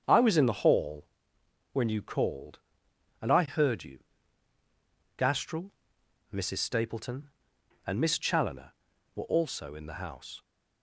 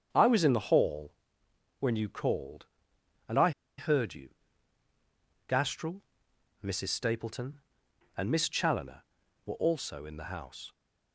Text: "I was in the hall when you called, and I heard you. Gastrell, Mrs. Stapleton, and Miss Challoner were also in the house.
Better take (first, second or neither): first